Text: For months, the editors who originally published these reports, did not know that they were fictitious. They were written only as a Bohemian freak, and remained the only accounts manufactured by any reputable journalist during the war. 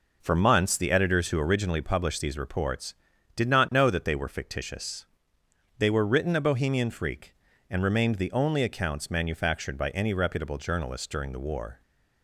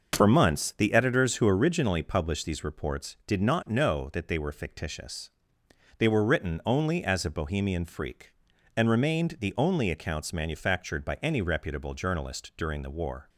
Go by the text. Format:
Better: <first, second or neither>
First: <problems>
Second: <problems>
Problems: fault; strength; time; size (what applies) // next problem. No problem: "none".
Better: second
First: skips "only as"; at 6.3 s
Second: none